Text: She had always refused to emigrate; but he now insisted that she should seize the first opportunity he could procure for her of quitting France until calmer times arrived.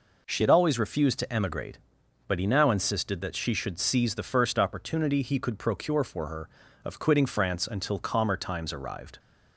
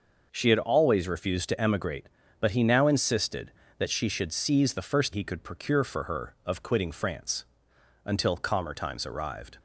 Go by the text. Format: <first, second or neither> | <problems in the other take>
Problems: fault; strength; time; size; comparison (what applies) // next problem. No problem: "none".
first | skips "opportunity"; at 5.1 s // pauses between "France" and "until"; noticeable; at 7.4 s; 0.62 s long